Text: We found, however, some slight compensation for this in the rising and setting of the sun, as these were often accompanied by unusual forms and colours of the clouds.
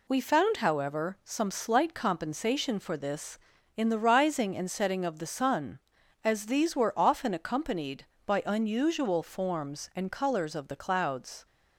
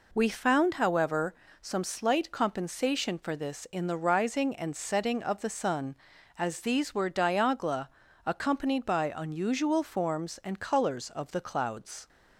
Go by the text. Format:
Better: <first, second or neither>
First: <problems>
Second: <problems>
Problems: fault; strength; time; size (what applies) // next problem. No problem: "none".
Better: first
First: none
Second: says "diagla" for "often"; at 7.1 s